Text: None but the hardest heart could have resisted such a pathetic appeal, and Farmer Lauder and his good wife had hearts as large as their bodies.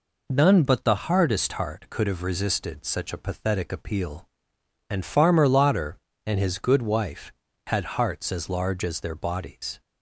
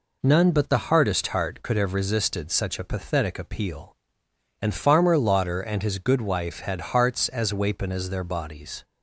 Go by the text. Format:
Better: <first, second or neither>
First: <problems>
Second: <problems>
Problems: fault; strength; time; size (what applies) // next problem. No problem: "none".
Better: first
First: none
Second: says "wapen" for "large"; at 7.5 s